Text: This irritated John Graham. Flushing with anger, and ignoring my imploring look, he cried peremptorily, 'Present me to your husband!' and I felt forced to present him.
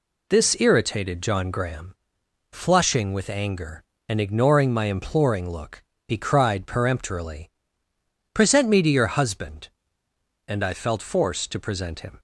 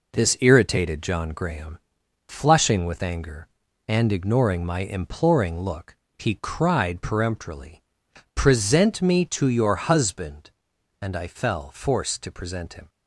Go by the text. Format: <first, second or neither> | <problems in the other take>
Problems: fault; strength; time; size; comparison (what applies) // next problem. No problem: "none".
first | says "fell" for "felt"; at 11.2 s